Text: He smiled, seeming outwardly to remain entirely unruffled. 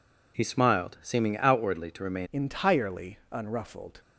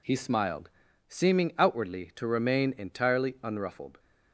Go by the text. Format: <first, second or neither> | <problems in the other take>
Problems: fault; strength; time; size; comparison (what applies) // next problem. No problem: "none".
second | changes voice at "entirely"; from 2.3 s on; 1.7 s long // pauses between "entirely" and "unruffled"; slight; at 3.1 s; 0.16 s long